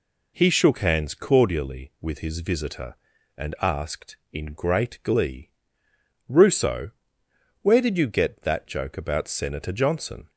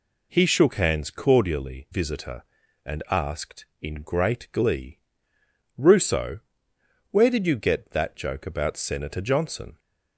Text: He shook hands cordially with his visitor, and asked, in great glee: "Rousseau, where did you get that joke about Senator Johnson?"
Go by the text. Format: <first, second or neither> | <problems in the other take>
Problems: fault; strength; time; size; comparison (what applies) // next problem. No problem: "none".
first | skips "with his"; at 1.8 s